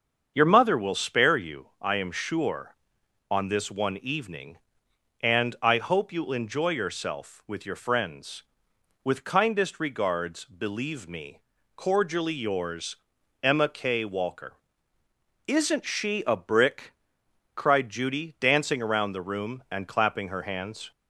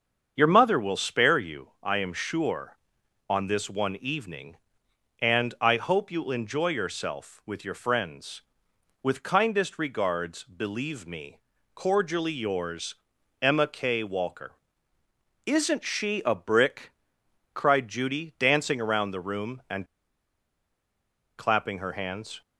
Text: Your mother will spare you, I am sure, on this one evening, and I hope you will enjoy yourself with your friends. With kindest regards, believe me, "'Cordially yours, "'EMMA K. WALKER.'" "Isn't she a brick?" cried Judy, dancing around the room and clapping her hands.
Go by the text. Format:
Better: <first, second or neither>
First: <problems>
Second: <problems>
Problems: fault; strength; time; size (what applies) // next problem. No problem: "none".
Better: first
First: starts louder than the rest; until 1.3 s; 7 dB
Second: starts louder than the rest; until 1.3 s; 7 dB // pauses between "and" and "clapping"; strong; at 19.8 s; 1.5 s long